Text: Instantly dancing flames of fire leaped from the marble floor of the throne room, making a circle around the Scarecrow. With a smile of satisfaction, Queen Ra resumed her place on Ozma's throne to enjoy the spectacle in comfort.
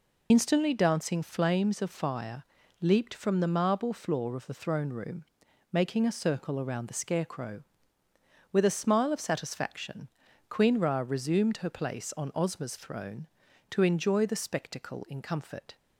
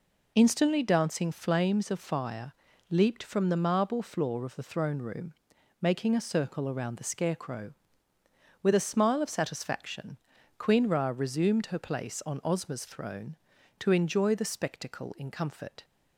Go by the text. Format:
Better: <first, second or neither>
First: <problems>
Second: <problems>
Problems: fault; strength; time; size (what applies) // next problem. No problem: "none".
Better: second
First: loses the start of "Instantly"; at 0.3 s; 35 ms // pauses between "fire" and "leaped"; at 2.4 s; 0.40 s long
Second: pauses between "fire" and "leaped"; at 2.5 s; 0.40 s long